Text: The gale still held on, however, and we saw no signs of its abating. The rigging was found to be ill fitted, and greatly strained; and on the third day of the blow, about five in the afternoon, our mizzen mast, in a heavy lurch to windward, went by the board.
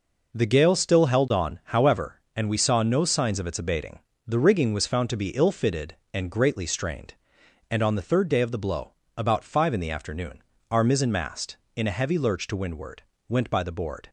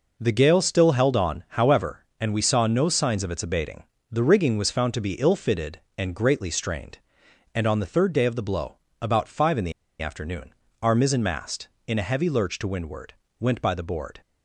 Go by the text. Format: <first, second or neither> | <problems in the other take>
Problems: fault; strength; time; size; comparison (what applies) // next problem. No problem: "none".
first | pauses between "the" and "afternoon"; slight; at 9.7 s; 0.30 s long